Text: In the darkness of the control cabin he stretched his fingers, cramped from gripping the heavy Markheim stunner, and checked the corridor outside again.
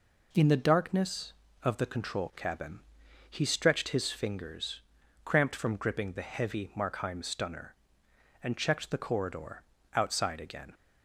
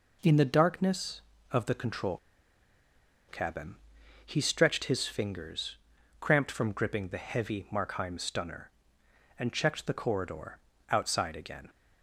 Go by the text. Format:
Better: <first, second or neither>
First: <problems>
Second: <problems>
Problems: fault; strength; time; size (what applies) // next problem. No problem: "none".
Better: first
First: pauses between "cabin" and "he"; noticeable; at 2.7 s; 0.50 s long // pauses between "corridor" and "outside"; slight; at 9.6 s; 0.32 s long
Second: pauses between "control" and "cabin"; at 2.1 s; 1.1 s long // pauses between "cabin" and "he"; noticeable; at 3.7 s; 0.50 s long // pauses between "corridor" and "outside"; slight; at 10.5 s; 0.32 s long